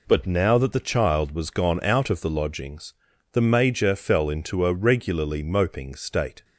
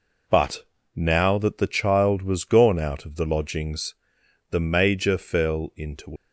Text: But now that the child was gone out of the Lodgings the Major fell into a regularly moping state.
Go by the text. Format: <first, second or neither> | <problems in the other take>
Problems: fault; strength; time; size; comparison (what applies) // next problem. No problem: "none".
first | pauses between "But" and "now"; slight; at 0.6 s; 0.28 s long // pauses between "Lodgings" and "the"; noticeable; at 3.9 s; 0.56 s long; also in the first // stops before "a regularly moping state"; at 6.1 s